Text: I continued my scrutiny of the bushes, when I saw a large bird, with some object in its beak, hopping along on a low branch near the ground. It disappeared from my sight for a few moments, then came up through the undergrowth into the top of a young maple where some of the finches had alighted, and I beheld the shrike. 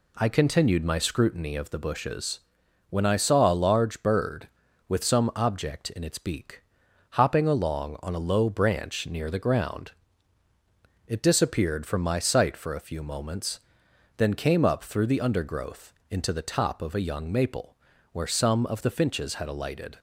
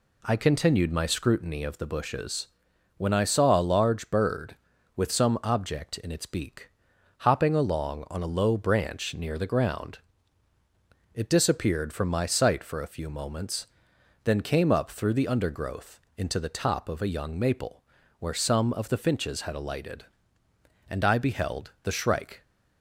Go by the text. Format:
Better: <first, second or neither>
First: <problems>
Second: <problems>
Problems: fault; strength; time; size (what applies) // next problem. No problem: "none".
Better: second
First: pauses between "undergrowth" and "into"; slight; at 15.9 s; 0.16 s long // pauses between "maple" and "where"; at 17.7 s; 0.38 s long // stops before "and I beheld the shrike"; at 19.9 s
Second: pauses between "undergrowth" and "into"; slight; at 16.0 s; 0.16 s long // pauses between "maple" and "where"; at 17.8 s; 0.38 s long